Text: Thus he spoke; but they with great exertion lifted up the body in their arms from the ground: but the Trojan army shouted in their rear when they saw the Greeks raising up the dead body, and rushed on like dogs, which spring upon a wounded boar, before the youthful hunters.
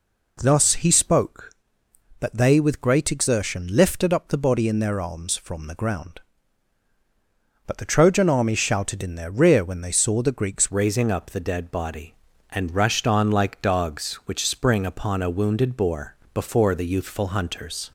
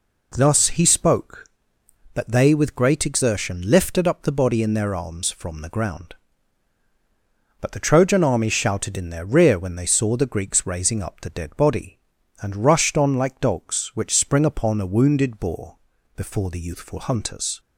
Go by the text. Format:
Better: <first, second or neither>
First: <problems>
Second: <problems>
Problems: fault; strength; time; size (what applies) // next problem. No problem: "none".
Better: second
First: changes voice at "raising"; from 10.7 s on; 7.2 s long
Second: none